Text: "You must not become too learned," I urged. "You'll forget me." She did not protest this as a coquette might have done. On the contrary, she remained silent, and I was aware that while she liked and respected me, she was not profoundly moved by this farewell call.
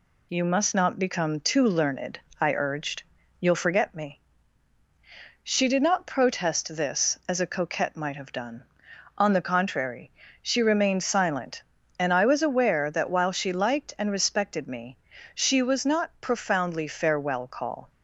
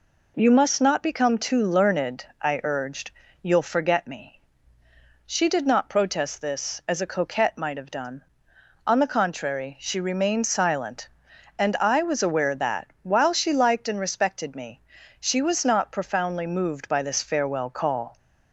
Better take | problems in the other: second | skips "moved by this"; at 16.8 s

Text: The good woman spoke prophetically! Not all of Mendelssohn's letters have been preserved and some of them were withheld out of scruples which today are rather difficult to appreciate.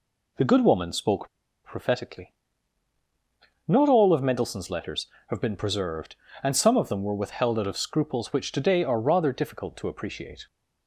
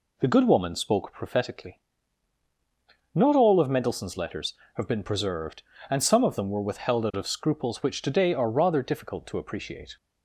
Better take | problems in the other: second | pauses between "spoke" and "prophetically"; at 1.2 s; 0.36 s long

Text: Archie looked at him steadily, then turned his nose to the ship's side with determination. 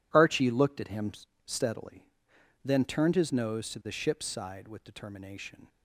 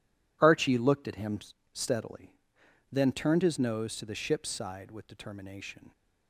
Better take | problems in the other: neither | pauses between "him" and "steadily"; slight; the same in both

